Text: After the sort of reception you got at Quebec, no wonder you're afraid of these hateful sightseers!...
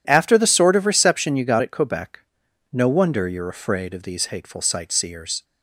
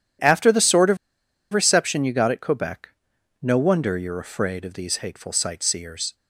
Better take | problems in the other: first | pauses between "of" and "reception"; noticeable; at 0.9 s; 0.55 s long

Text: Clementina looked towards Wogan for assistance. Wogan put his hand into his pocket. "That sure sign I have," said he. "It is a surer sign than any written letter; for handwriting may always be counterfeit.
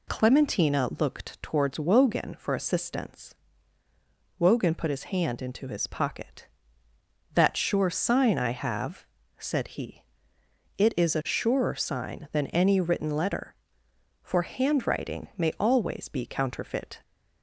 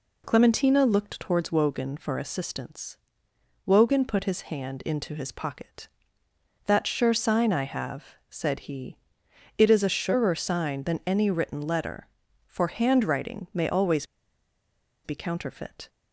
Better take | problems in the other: first | pauses between "always" and "be"; at 14.0 s; 0.98 s long

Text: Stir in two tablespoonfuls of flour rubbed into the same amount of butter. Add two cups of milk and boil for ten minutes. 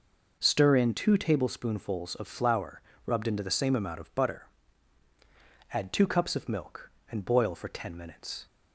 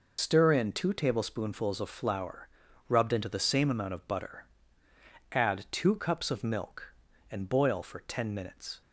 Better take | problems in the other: first | loses the start of "Stir"; at 0.1 s; 100 ms // pauses between "flour" and "rubbed"; at 2.4 s; 0.40 s long; slight in the first

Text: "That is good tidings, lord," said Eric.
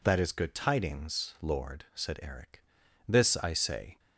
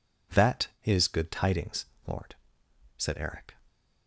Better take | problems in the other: second | goes on to say "This I say"; noticeable; from 3.0 s on; 0.92 s long

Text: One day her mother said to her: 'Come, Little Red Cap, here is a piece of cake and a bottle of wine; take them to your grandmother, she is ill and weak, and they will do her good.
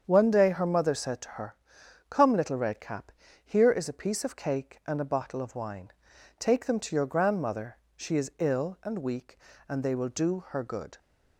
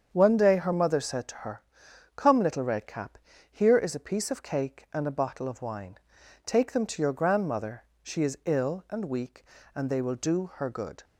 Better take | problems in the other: neither | starts louder than the rest; strong; the same in both

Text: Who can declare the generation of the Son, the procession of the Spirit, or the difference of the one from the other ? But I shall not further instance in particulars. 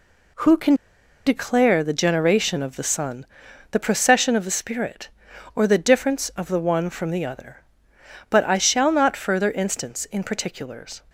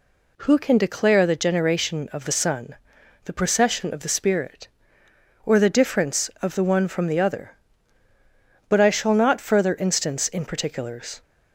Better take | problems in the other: second | pauses between "can" and "declare"; noticeable; at 0.7 s; 0.52 s long

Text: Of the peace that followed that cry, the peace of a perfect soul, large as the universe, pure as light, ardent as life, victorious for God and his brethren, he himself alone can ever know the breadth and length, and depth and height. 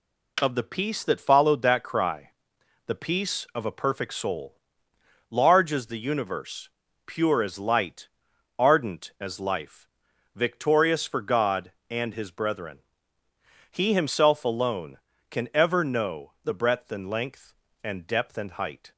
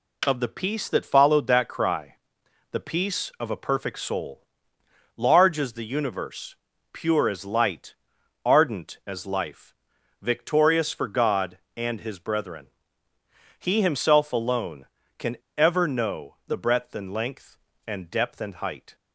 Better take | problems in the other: first | pauses between "can" and "ever"; slight; at 15.3 s; 0.21 s long

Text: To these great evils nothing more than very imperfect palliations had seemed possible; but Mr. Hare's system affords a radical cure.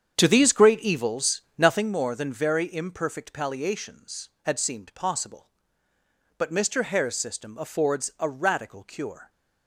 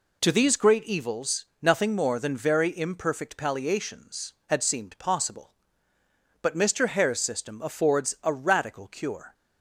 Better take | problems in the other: second | starts louder than the rest; strong; until 1.9 s; 8 dB // pauses between "evils" and "nothing"; slight; at 1.4 s; 0.16 s long; slight in the second

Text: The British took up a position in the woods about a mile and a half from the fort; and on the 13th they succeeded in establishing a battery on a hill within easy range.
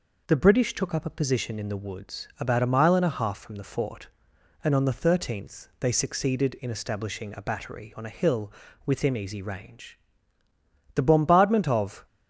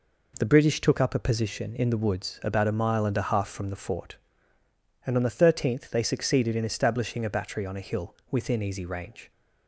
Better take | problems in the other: second | pauses between "hill" and "within"; slight; at 8.4 s; 0.36 s long // goes on to say "The bombardment of"; noticeable; from 10.9 s on; 1.1 s long

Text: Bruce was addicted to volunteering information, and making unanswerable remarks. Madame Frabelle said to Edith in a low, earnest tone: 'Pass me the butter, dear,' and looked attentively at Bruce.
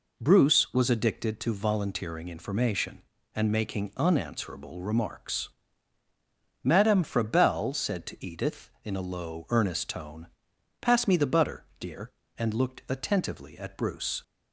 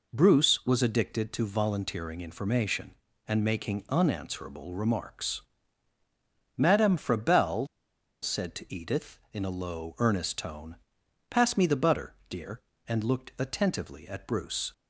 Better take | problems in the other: first | pauses between "Frabelle" and "said"; noticeable; at 7.6 s; 0.57 s long

